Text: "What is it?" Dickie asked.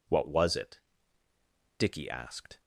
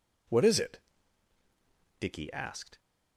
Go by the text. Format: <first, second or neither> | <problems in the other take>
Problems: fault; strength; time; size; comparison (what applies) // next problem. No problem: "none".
second | says "was" for "is"; at 0.2 s